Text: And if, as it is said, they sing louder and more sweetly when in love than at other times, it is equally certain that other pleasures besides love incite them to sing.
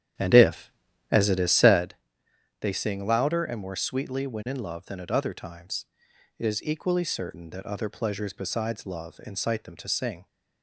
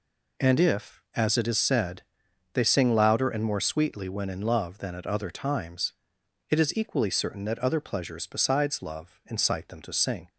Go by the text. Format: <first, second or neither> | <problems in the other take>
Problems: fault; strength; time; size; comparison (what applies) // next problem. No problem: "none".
second | starts louder than the rest; strong; until 1.9 s; 10 dB